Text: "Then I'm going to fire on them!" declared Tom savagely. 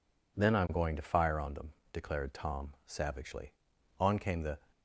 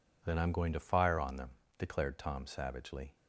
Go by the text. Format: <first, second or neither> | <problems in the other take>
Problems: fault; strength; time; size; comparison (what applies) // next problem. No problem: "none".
second | goes on to say "On came the"; from 3.9 s on; 0.60 s long